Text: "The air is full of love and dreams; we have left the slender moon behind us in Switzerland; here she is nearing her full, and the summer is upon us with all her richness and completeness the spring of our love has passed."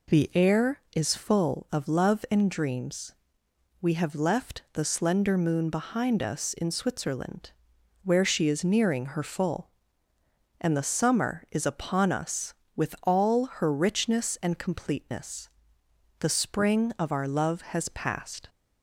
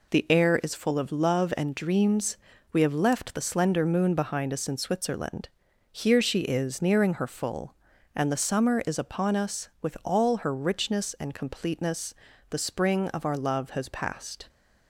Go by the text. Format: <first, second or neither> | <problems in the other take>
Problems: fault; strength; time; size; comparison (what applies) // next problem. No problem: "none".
second | says "where" for "here"; at 8.0 s // pauses between "all" and "her"; slight; at 13.4 s; 0.16 s long // pauses between "completeness" and "the"; noticeable; at 15.4 s; 0.72 s long; slight in the second